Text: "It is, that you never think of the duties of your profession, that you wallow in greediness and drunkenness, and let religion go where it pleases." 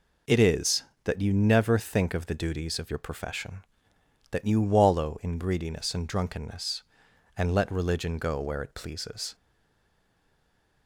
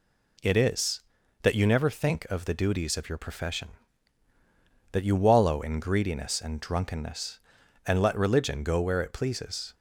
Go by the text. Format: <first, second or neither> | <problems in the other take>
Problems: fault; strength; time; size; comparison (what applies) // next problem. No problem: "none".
second | stays silent after the last word; noticeable; from 9.3 s on; 1.5 s long